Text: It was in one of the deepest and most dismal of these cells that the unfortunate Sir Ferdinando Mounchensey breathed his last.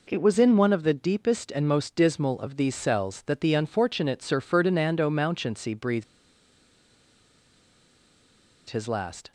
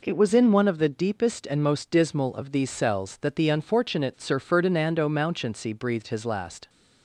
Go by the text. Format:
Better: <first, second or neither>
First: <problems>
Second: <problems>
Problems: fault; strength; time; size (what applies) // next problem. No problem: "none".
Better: second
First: pauses between "breathed" and "his"; strong; at 6.0 s; 2.6 s long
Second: none